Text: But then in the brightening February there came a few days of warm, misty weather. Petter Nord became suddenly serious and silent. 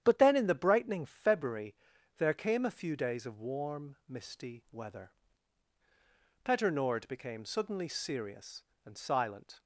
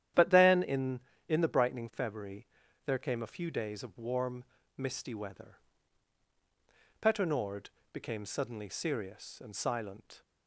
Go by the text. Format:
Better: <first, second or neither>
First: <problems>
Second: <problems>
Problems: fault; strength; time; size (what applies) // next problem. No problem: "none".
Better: first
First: starts louder than the rest; strong; until 1.0 s; 9.5 dB // pauses between "February" and "there"; at 1.7 s; 0.42 s long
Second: starts louder than the rest; strong; until 1.4 s; 10.5 dB // says "in" twice; at 1.2 s // pauses between "February" and "there"; at 2.4 s; 0.38 s long // pauses between "Nord" and "became"; slight; at 7.6 s; 0.22 s long